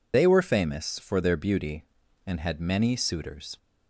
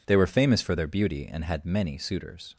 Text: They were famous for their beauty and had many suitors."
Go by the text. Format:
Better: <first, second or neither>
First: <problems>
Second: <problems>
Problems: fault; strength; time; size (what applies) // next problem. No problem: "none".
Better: second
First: loses the start of "They"; at 0.1 s; 125 ms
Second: none